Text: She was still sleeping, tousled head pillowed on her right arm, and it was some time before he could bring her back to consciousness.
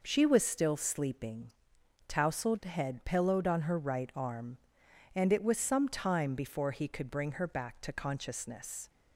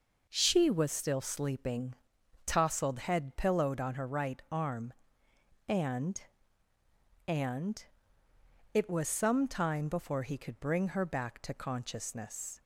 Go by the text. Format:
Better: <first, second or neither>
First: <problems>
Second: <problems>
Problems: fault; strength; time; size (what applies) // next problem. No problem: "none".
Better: first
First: none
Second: says "and" twice; at 7.2 s